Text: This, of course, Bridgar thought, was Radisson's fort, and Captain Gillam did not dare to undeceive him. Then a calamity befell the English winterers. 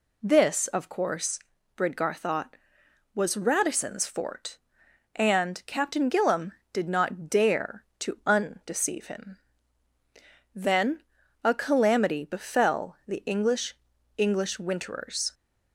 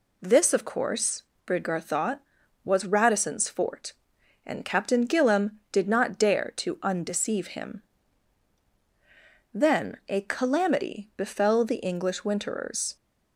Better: second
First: pauses between "Then" and "a"; at 11.0 s; 0.42 s long // says "English" twice; at 14.1 s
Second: none

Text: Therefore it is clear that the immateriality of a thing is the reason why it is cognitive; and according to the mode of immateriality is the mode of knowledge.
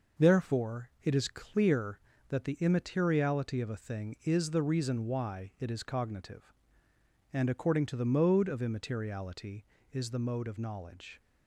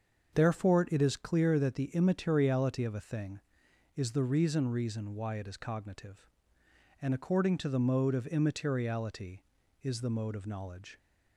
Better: first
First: none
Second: starts louder than the rest; until 1.3 s; 6.5 dB // says "reason" twice; at 4.6 s

